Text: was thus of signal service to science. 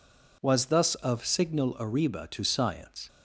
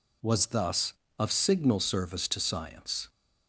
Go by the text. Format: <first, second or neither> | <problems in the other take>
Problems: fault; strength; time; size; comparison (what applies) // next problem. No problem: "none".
second | says "arriba" for "service"; at 1.8 s